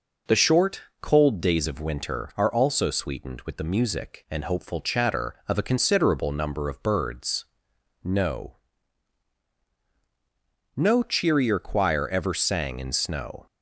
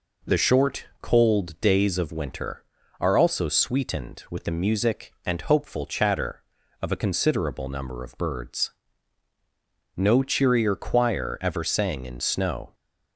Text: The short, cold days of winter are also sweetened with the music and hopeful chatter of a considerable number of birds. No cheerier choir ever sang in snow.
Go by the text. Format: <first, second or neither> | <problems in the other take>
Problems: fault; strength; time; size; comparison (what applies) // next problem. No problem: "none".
second | says "No" twice; at 10.7 s